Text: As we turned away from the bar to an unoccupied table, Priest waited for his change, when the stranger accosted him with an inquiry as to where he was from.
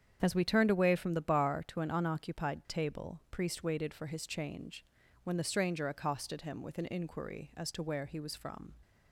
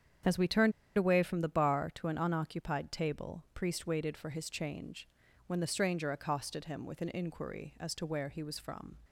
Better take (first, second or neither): first